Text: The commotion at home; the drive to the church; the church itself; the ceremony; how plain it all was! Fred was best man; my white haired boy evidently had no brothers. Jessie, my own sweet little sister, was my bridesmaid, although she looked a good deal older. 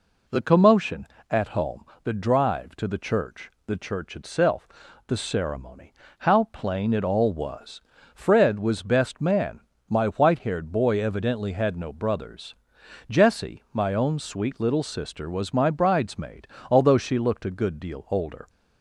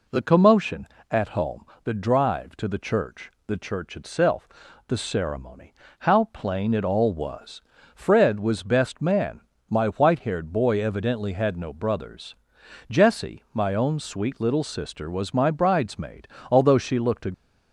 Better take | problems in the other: first | stops before "good deal older"; at 17.3 s

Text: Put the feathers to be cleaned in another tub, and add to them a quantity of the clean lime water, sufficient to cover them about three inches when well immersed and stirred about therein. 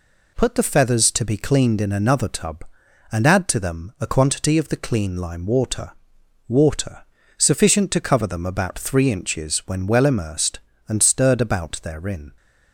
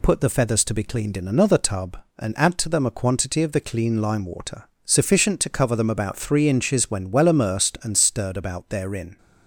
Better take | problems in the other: second | says "water" twice; at 6.4 s

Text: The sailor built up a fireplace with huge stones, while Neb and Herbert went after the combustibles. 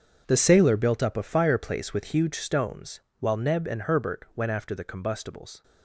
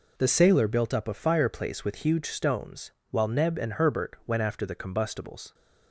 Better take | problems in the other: second | gets quieter; strong; throughout; 13.5 dB

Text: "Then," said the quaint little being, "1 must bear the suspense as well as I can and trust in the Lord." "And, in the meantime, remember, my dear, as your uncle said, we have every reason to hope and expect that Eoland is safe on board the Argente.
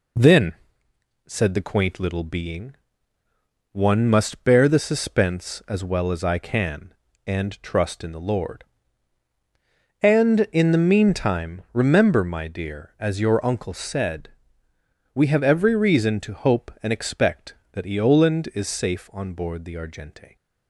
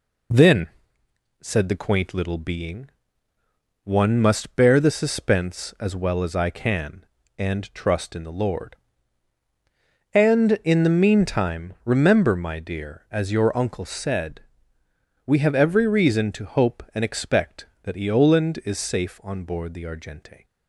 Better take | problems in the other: neither | none

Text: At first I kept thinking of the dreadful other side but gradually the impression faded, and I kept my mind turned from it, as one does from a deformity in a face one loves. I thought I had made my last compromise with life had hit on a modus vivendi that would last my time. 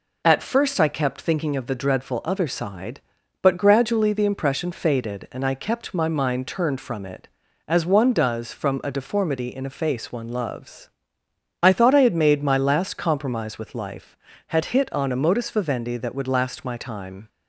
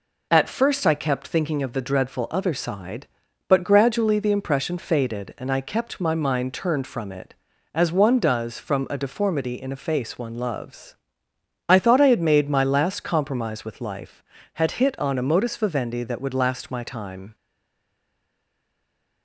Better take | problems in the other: first | stays silent after the last word; noticeable; from 17.3 s on; 1.9 s long

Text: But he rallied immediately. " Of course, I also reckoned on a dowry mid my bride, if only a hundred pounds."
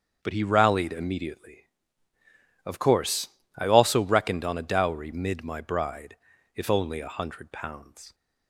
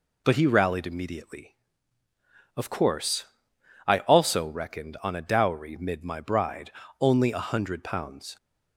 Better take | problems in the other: first | skips "if"; at 6.8 s

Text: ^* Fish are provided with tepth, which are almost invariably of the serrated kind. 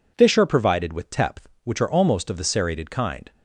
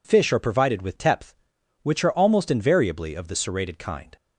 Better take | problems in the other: second | skips "invariably"; at 2.2 s

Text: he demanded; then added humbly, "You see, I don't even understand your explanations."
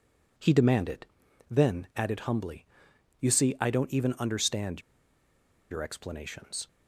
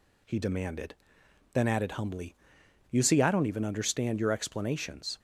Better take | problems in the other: second | pauses between "understand" and "your"; noticeable; at 4.8 s; 0.90 s long

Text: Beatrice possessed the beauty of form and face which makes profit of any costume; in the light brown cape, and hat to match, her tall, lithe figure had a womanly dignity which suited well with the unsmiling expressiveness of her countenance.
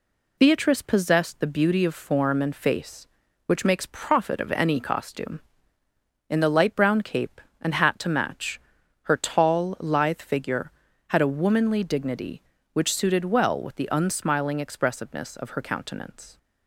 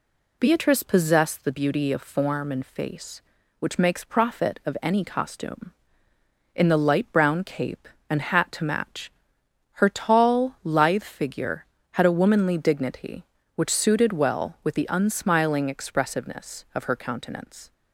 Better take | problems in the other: neither | none

